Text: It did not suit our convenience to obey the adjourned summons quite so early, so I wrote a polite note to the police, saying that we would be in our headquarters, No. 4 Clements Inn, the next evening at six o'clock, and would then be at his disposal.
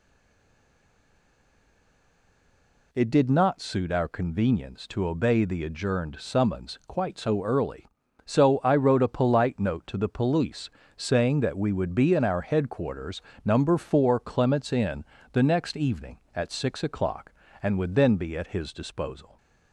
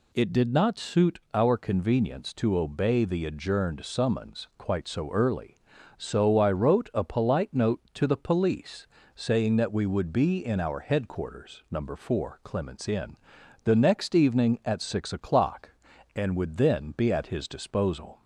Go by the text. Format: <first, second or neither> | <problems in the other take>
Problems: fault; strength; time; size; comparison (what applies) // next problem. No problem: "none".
second | stays silent before the first word; strong; until 2.9 s; 2.9 s long